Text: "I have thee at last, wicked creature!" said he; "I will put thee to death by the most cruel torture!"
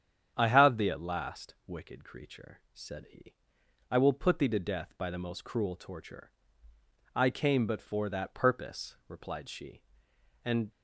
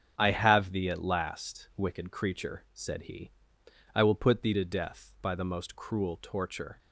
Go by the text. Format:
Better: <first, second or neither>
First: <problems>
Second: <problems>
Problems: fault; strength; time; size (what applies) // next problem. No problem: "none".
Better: second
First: starts louder than the rest; strong; until 1.3 s; 8.5 dB // goes on to say "I came but for that purpose replied she and"; strong; from 7.1 s on; 3.5 s long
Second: starts louder than the rest; strong; until 1.1 s; 7 dB